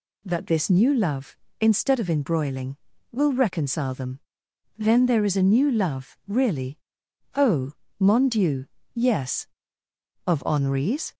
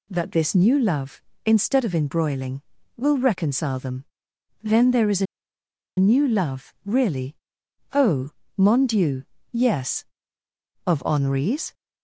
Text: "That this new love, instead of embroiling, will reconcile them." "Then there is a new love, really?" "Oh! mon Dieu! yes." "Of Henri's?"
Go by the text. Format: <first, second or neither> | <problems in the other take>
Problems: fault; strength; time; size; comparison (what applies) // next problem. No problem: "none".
first | pauses between "a" and "new"; noticeable; at 5.2 s; 0.73 s long